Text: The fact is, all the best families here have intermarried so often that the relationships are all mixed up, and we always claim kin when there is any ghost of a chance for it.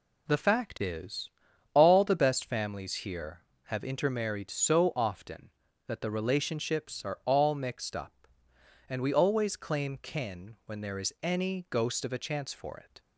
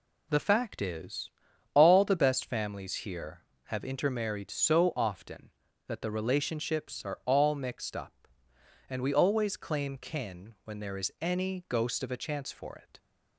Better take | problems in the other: neither | none

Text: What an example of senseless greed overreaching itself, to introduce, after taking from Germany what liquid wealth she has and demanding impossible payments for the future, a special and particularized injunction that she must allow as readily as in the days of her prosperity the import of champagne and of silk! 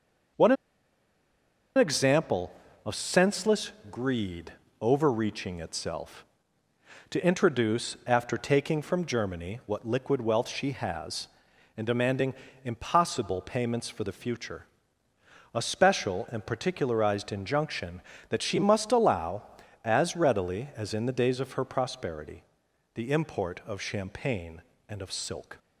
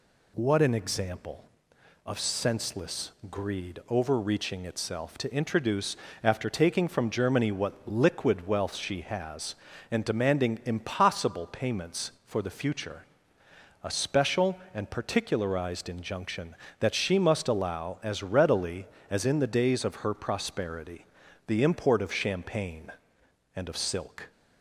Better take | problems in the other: second | pauses between "an" and "example"; at 0.5 s; 1.2 s long // pauses between "senseless" and "greed"; slight; at 3.7 s; 0.18 s long; slight in the second // pauses between "greed" and "overreaching"; slight; at 4.5 s; 0.26 s long // pauses between "demanding" and "impossible"; slight; at 12.3 s; 0.30 s long // pauses between "prosperity" and "the"; noticeable; at 22.4 s; 0.52 s long; also in the second

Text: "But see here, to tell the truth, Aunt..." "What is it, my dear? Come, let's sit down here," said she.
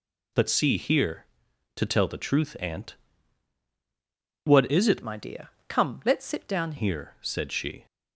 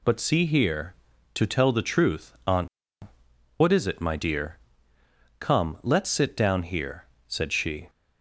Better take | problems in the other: second | changes voice from "my" to "down"; from 5.0 to 6.7 s; 1.7 s long

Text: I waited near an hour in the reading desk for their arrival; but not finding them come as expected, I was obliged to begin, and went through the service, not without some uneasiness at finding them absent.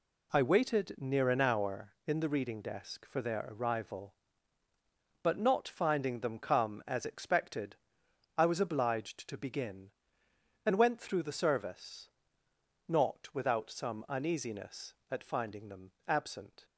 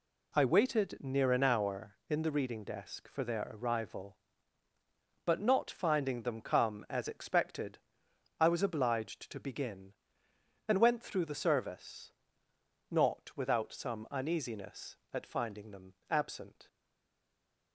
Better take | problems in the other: first | pauses between "them" and "absent"; slight; at 15.9 s; 0.16 s long; slight in the first // stays silent after the last word; from 16.6 s on; 1.1 s long

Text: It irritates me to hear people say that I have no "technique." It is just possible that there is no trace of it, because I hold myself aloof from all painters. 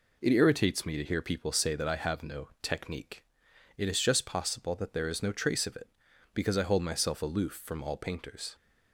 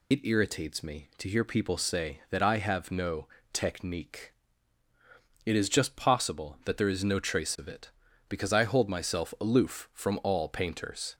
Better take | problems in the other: first | loses the start of "It"; at 0.1 s; 45 ms // pauses between "no" and "technique"; slight; at 3.2 s; 0.26 s long

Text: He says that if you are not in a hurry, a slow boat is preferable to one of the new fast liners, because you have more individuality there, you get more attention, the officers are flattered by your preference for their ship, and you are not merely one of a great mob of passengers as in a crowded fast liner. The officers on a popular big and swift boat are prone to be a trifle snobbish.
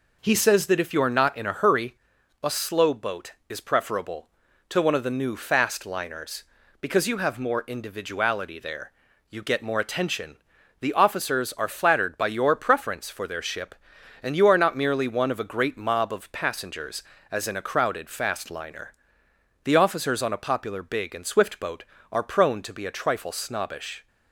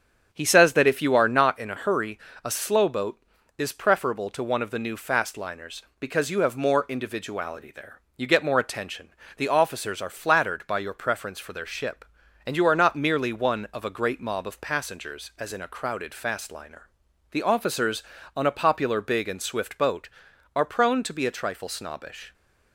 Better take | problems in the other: first | starts louder than the rest; strong; until 1.6 s; 7.5 dB

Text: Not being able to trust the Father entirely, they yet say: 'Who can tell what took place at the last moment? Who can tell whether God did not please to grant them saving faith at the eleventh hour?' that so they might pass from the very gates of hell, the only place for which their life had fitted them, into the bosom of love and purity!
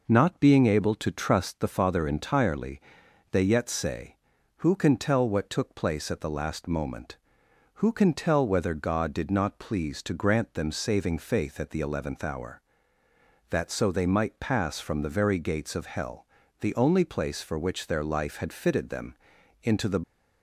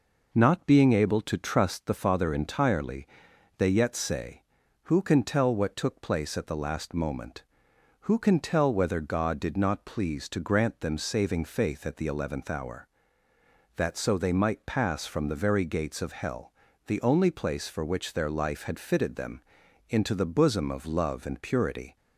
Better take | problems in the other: second | stops before "bosom of love and purity"; at 20.0 s

